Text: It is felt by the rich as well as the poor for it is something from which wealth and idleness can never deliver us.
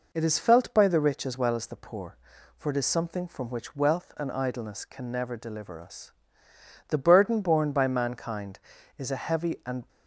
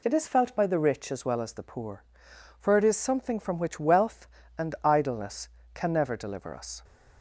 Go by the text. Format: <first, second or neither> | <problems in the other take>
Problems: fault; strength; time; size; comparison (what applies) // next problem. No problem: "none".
second | goes on to say "The burden borne by mankind is a heavy and"; strong; from 6.8 s on; 3.0 s long